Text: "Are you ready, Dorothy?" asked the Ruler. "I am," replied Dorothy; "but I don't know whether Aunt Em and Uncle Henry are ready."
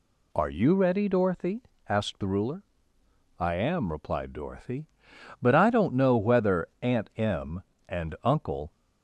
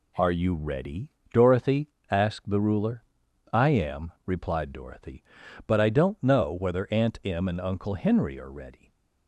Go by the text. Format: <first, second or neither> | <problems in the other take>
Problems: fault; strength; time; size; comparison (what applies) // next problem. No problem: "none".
second | stops before "Henry are ready"; at 8.7 s